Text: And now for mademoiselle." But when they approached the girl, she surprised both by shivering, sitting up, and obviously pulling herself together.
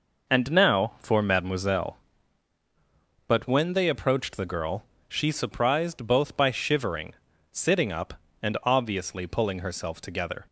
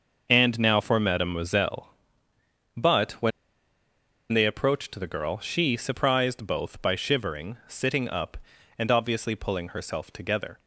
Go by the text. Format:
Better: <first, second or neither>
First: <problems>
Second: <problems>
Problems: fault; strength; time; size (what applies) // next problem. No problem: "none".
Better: first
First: none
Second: starts louder than the rest; noticeable; until 1.3 s; 6 dB // pauses between "when" and "they"; at 3.3 s; 1.0 s long